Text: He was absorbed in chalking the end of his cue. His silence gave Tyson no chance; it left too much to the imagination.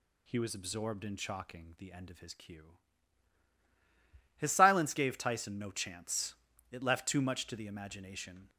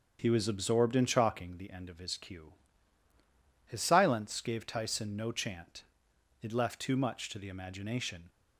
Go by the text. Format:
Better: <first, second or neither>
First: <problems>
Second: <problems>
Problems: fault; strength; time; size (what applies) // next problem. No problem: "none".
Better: first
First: none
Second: starts louder than the rest; until 1.2 s; 6.5 dB // says "chant" for "chance"; at 5.3 s